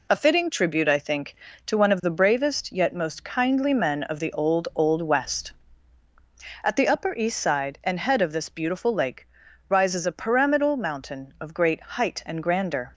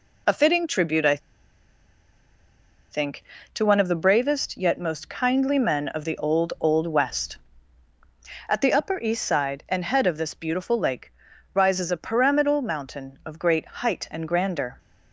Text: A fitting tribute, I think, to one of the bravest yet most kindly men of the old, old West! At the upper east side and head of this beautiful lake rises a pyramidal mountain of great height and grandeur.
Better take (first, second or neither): first